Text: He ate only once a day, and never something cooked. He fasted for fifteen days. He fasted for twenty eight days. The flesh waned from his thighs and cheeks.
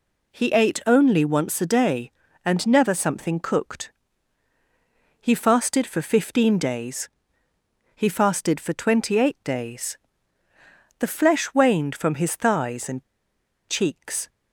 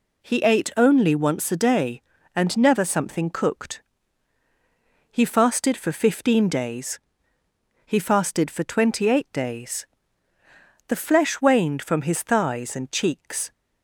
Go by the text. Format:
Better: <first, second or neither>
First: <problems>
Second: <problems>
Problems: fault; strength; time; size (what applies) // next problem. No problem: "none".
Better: second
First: pauses between "and" and "cheeks"; noticeable; at 13.0 s; 0.64 s long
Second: none